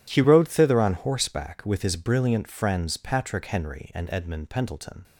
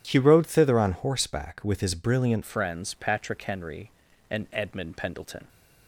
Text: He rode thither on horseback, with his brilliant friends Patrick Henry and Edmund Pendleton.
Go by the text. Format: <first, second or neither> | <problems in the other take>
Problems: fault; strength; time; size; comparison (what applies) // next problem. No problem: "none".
first | changes voice at "friends"; from 2.4 s on; 3.0 s long